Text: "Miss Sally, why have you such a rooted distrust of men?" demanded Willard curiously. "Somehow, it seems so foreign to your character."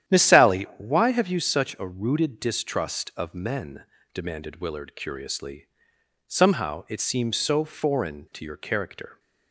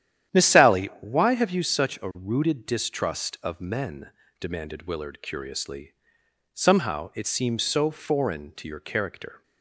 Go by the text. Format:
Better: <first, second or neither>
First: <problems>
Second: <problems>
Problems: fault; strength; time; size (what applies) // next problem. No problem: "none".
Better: neither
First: starts louder than the rest; strong; until 1.2 s; 10.5 dB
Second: starts louder than the rest; strong; until 1.4 s; 10.5 dB